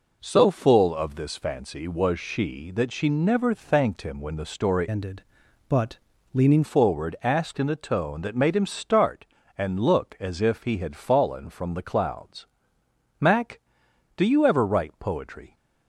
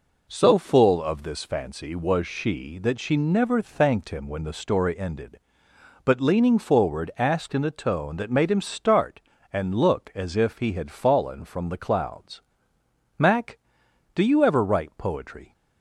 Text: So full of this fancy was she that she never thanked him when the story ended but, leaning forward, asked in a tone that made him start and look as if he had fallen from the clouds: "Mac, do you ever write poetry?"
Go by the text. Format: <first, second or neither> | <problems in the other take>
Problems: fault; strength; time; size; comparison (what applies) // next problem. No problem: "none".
second | changes voice from "ended" to "leaning"; from 4.8 to 6.6 s; 1.8 s long